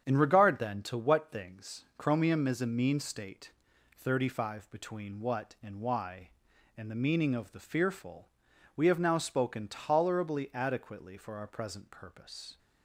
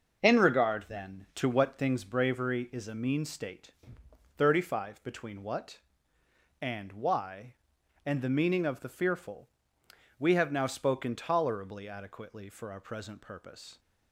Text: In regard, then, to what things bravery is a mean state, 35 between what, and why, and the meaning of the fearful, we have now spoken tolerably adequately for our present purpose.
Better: second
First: starts louder than the rest; strong; until 1.0 s; 8 dB // says "chromium" for "bravery"; at 1.9 s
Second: none

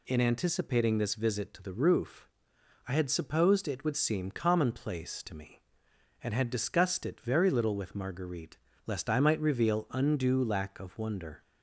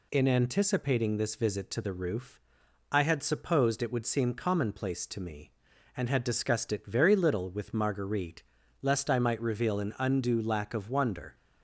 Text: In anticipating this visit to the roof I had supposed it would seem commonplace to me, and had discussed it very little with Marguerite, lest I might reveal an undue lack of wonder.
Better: second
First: pauses between "roof" and "I"; noticeable; at 2.2 s; 0.60 s long // skips "an"; at 9.8 s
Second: pauses between "roof" and "I"; noticeable; at 2.4 s; 0.50 s long

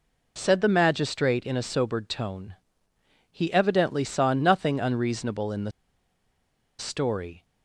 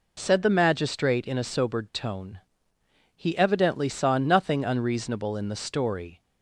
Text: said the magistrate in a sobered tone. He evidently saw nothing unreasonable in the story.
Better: second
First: pauses between "the" and "story"; at 5.7 s; 1.0 s long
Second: none

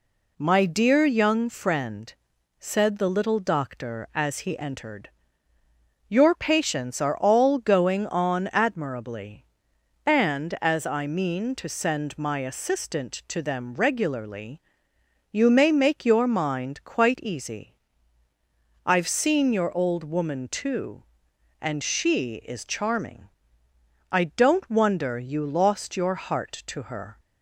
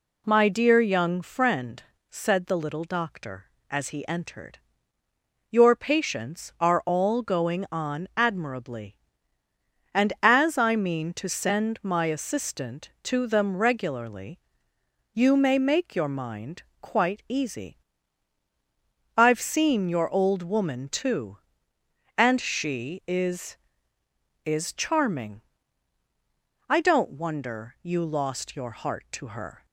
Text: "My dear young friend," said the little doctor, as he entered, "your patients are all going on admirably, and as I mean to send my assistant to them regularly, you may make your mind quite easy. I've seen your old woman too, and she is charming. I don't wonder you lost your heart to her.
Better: first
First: none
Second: pauses between "mind" and "quite"; slight; at 16.6 s; 0.18 s long // says "is" twice; at 24.4 s

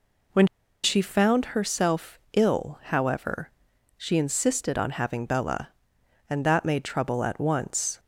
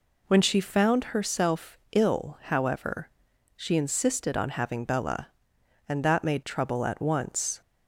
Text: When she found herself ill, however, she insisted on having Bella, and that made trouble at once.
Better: second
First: pauses between "When" and "she"; at 0.4 s; 0.38 s long // pauses between "herself" and "ill"; slight; at 2.1 s; 0.16 s long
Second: pauses between "herself" and "ill"; slight; at 1.7 s; 0.16 s long

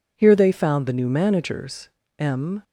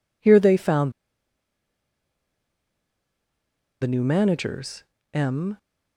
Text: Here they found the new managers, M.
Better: first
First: none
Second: pauses between "found" and "the"; strong; at 0.9 s; 2.9 s long

